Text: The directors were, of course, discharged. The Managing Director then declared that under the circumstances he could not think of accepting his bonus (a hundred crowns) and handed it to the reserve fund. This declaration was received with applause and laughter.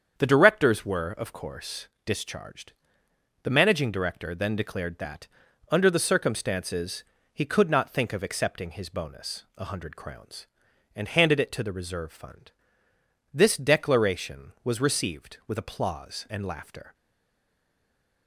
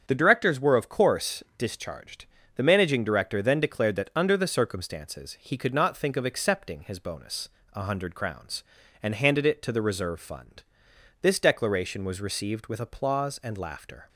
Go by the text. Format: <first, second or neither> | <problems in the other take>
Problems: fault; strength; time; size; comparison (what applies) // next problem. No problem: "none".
second | starts louder than the rest; strong; until 1.2 s; 7.5 dB; strong in the second // pauses between "that" and "under"; at 5.2 s; 0.42 s long // pauses between "circumstances" and "he"; slight; at 7.0 s; 0.30 s long // stays silent after the last word; noticeable; from 16.9 s on; 1.3 s long